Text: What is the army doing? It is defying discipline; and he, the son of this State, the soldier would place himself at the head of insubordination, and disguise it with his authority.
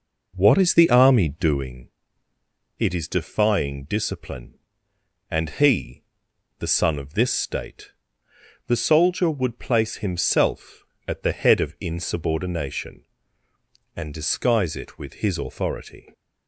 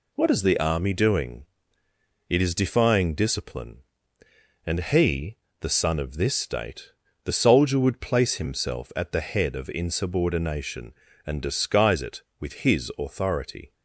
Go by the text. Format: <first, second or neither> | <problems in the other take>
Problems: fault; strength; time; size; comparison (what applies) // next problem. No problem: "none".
second | starts louder than the rest; noticeable; until 1.7 s; 4.5 dB